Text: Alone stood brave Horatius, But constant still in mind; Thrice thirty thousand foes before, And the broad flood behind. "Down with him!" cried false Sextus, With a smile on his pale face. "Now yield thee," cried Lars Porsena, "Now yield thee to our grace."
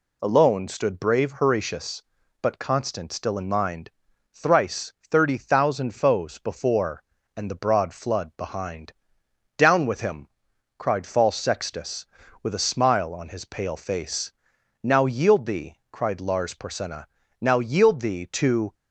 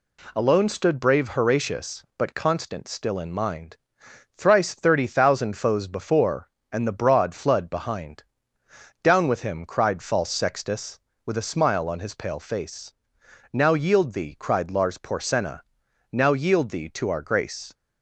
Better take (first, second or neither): second